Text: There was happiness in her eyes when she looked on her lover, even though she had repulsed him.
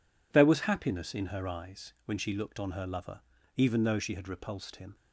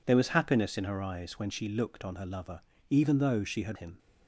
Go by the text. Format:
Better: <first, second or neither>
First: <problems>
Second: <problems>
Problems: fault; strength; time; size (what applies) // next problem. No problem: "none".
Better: first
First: none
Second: skips "repulsed"; at 3.7 s